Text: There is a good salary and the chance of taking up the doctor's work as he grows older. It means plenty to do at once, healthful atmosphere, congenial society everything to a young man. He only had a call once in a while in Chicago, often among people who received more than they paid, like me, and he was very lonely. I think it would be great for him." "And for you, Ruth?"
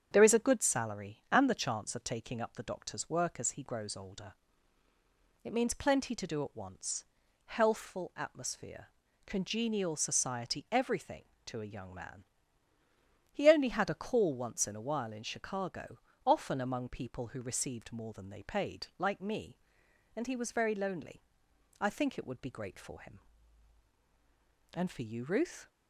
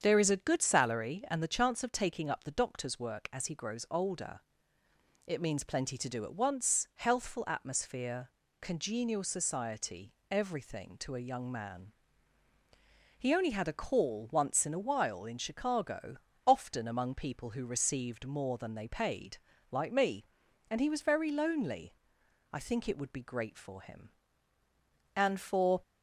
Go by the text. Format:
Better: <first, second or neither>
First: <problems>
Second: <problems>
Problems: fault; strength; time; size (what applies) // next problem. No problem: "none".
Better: first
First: starts louder than the rest; strong; until 1.1 s; 8 dB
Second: starts louder than the rest; strong; until 1.0 s; 7.5 dB // pauses between "society" and "everything"; slight; at 10.1 s; 0.18 s long // stops before "you Ruth"; at 25.8 s